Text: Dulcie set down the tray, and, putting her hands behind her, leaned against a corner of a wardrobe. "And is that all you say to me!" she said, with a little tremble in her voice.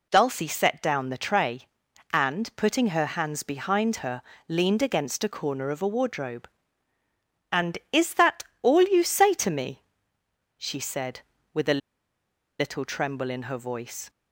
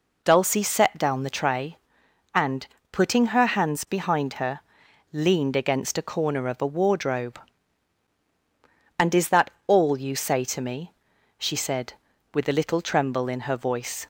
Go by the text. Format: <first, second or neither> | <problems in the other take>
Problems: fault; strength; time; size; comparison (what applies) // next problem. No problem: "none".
second | pauses between "that" and "all"; slight; at 8.4 s; 0.20 s long; slight in the second // pauses between "a" and "little"; noticeable; at 11.8 s; 0.79 s long